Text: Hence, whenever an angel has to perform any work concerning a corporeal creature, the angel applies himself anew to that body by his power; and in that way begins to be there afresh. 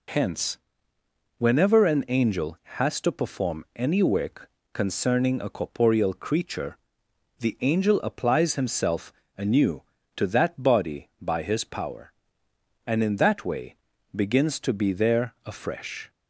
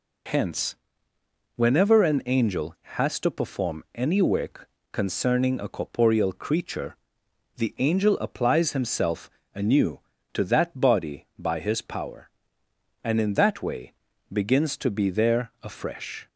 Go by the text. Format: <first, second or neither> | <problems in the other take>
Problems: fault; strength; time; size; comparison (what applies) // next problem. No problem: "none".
neither | pauses between "work" and "concerning"; slight; the same in both // pauses between "himself" and "anew"; slight; the same in both // pauses between "way" and "begins"; the same in both